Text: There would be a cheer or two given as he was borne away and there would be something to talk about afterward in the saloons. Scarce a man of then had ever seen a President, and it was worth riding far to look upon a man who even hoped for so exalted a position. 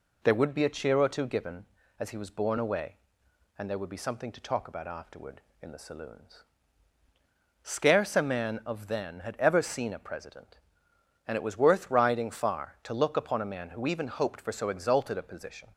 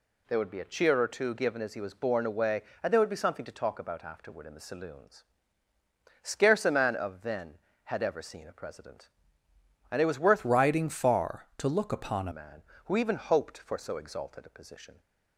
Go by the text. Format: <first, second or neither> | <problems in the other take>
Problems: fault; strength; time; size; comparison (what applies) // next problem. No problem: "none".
first | changes voice from "riding" to "a"; from 10.4 to 12.3 s; 1.9 s long